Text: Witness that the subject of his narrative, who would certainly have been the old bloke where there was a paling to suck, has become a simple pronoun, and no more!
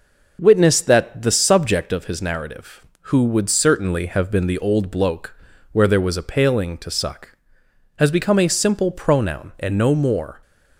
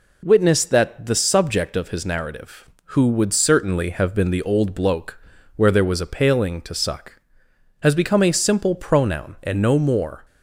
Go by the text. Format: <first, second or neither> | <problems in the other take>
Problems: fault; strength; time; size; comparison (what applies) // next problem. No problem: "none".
second | starts louder than the rest; noticeable; until 2.0 s; 5.5 dB // pauses between "bloke" and "where"; at 5.3 s; 0.38 s long; also in the second